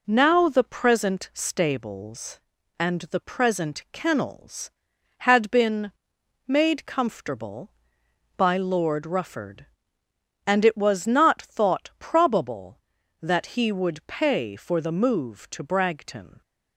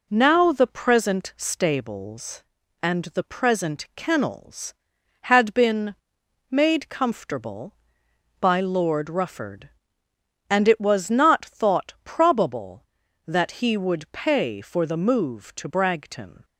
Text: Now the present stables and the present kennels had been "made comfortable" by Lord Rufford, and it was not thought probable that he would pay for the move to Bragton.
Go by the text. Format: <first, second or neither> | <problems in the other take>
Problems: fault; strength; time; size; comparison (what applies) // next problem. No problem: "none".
neither | pauses between "been" and "made"; noticeable; the same in both